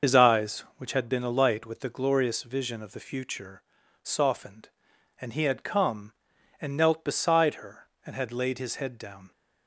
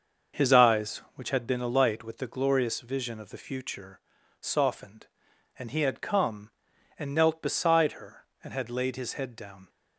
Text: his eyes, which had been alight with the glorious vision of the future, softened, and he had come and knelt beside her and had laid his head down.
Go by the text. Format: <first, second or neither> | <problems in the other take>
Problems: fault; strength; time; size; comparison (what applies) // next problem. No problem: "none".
second | loses the start of "his"; at 0.0 s; 70 ms // starts louder than the rest; until 1.1 s; 6 dB; also in the second